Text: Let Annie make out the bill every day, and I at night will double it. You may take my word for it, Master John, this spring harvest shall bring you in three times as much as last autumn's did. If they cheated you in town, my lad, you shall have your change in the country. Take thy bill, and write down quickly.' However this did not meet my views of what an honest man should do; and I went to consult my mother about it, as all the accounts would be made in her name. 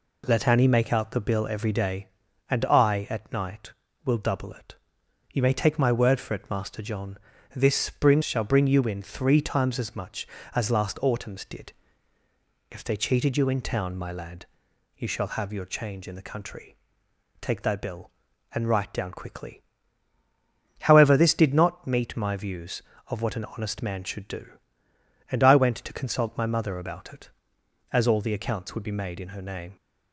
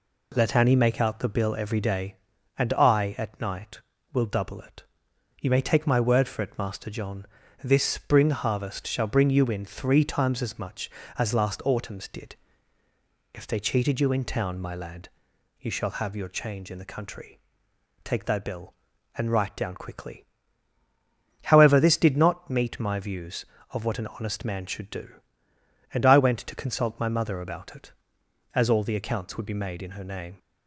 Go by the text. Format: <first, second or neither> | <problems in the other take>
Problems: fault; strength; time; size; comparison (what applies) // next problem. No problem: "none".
second | skips "harvest"; at 8.2 s